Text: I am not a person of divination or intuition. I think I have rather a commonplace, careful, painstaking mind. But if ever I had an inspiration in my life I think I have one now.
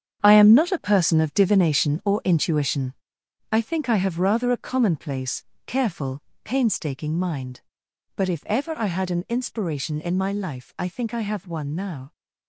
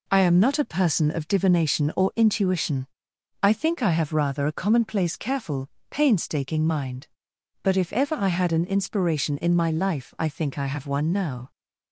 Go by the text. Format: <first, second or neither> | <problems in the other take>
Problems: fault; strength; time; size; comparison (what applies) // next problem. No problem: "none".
second | gets quieter; strong; throughout; 10 dB